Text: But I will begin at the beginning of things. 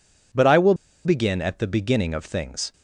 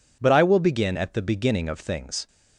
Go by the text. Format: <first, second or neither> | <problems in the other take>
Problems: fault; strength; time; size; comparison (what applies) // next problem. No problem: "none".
second | pauses between "will" and "begin"; slight; at 0.7 s; 0.31 s long